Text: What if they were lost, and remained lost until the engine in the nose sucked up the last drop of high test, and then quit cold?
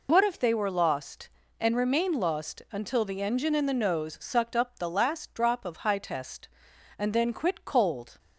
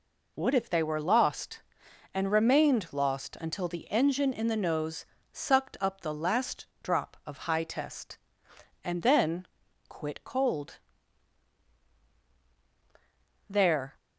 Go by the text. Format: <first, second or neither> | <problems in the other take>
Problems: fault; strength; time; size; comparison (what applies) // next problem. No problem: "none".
first | pauses between "nose" and "sucked"; slight; at 5.0 s; 0.28 s long // pauses between "last" and "drop"; slight; at 6.6 s; 0.18 s long // pauses between "then" and "quit"; at 9.4 s; 0.40 s long // goes on to say "There"; slight; from 13.4 s on; 0.46 s long